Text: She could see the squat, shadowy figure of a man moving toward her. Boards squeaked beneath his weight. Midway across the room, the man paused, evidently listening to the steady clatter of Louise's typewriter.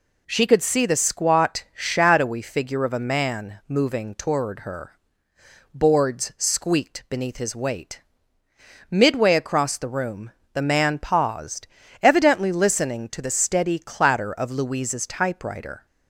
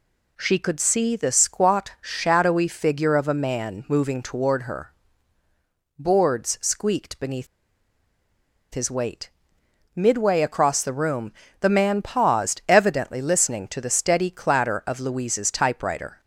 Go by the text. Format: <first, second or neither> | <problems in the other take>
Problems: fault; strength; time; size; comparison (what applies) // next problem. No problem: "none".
first | pauses between "beneath" and "his"; strong; at 7.4 s; 1.2 s long